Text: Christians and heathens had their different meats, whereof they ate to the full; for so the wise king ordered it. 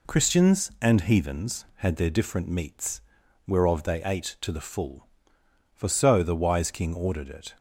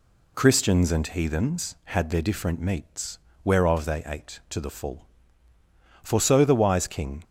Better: first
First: none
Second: stops before "ordered it"; at 7.2 s

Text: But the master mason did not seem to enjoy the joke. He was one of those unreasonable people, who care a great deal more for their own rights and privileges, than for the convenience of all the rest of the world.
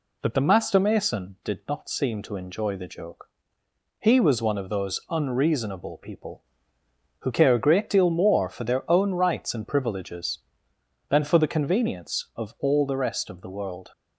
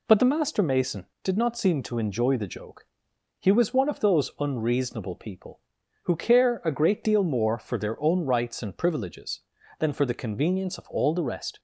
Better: first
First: none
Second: stops before "of the world"; at 11.5 s

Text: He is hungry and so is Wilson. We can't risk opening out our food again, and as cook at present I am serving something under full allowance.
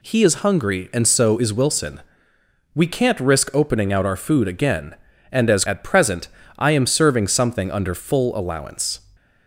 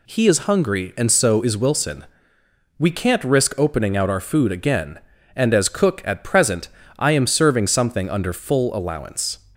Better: second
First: skips "cook"; at 5.6 s // pauses between "present" and "I"; slight; at 6.2 s; 0.30 s long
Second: pauses between "present" and "I"; slight; at 6.6 s; 0.30 s long

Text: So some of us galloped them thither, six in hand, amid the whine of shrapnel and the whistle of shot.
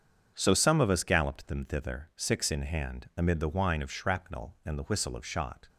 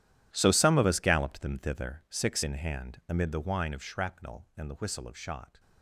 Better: first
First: starts louder than the rest; strong; until 1.3 s; 7 dB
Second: gets quieter; strong; throughout; 16.5 dB // starts louder than the rest; strong; until 1.3 s; 11.5 dB

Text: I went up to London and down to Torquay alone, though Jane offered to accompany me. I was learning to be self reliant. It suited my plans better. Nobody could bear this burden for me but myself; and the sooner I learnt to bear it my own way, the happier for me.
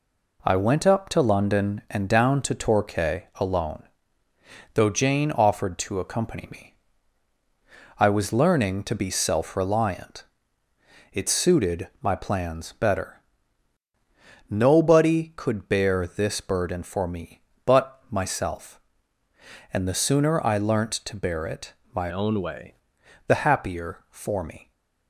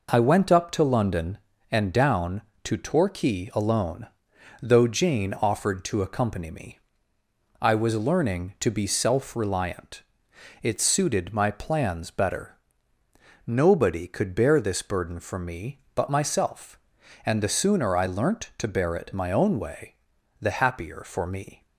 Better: second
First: pauses between "it" and "my"; slight; at 21.7 s; 0.18 s long // changes voice from "own" to "way"; from 22.1 to 22.7 s; 0.6 s long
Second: none

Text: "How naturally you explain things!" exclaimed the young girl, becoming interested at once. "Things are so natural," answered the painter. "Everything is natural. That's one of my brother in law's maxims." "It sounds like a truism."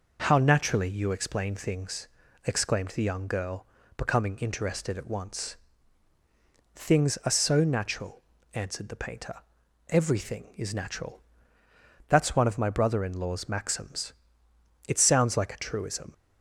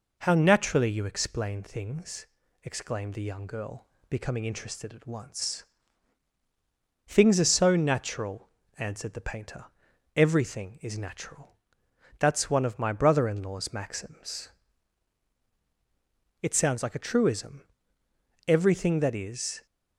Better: first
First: none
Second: goes on to say "Everything that is"; noticeable; from 18.4 s on; 1.1 s long

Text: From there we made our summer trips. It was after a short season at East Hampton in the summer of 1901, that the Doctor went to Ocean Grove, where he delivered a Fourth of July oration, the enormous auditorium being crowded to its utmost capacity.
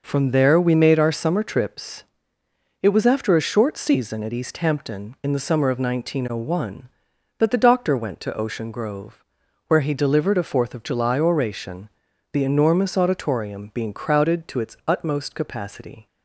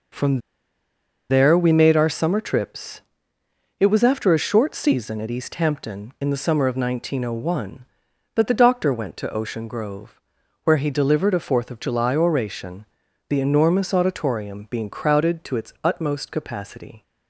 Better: first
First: none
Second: pauses between "From" and "there"; noticeable; at 0.4 s; 0.89 s long

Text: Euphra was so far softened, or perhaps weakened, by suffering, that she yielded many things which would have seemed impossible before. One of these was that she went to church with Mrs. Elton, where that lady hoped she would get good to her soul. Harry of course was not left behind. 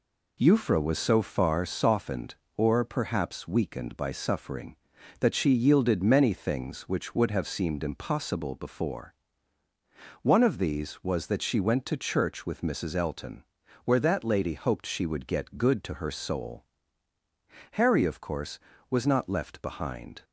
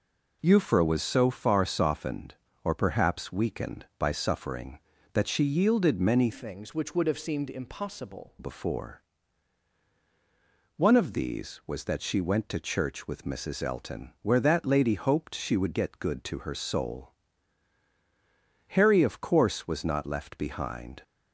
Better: first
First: none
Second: changes voice from "things" to "impossible"; from 6.3 to 8.3 s; 2.0 s long

